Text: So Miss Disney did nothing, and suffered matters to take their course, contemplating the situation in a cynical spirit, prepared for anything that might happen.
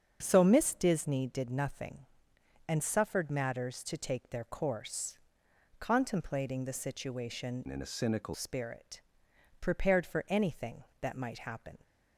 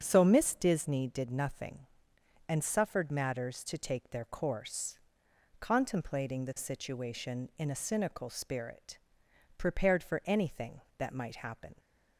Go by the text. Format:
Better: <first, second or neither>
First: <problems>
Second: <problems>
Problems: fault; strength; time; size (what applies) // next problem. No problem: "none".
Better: second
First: starts louder than the rest; strong; until 1.2 s; 7 dB // changes voice from "in" to "cynical"; from 7.6 to 8.3 s; 0.7 s long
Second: starts louder than the rest; strong; until 1.0 s; 7 dB